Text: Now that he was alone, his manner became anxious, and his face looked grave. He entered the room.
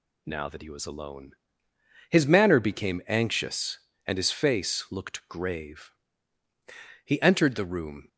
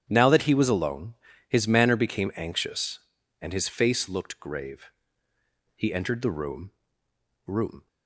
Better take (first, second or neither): first